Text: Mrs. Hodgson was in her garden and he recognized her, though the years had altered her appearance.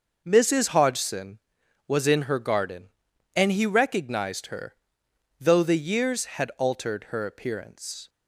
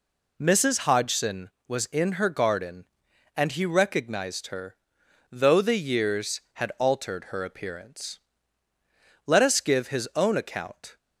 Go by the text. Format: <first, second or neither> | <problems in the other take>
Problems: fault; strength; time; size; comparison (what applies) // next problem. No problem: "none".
first | goes on to say "Let us give his own account"; strong; from 9.2 s on; 1.7 s long